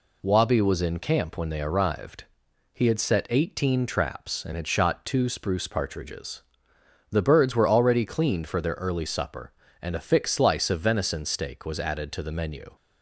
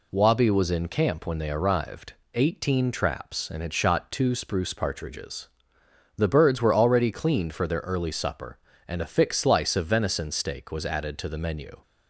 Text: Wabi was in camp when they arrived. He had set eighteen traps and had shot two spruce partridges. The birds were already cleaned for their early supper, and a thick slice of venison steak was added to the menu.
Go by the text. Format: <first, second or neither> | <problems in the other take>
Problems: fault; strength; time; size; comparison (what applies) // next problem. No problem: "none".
first | skips "He had set"; at 2.2 s